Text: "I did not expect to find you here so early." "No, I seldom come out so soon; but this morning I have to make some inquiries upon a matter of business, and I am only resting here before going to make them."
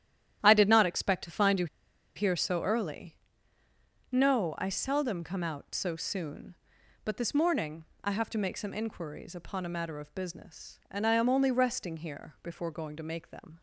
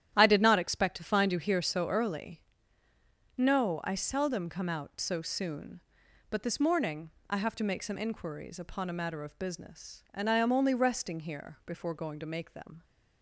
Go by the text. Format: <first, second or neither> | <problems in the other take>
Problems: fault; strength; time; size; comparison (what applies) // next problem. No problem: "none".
second | starts louder than the rest; strong; until 1.4 s; 11 dB; strong in the second // pauses between "you" and "here"; noticeable; at 1.6 s; 0.48 s long // pauses between "morning" and "I"; slight; at 7.8 s; 0.20 s long; slight in the second